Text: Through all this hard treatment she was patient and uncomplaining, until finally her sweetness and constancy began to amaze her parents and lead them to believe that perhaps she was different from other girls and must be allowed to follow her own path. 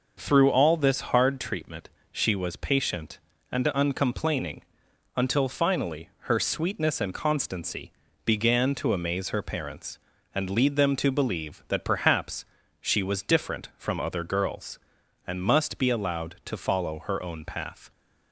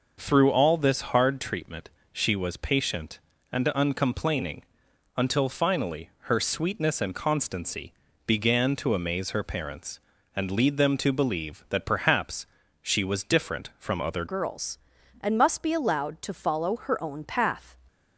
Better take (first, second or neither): first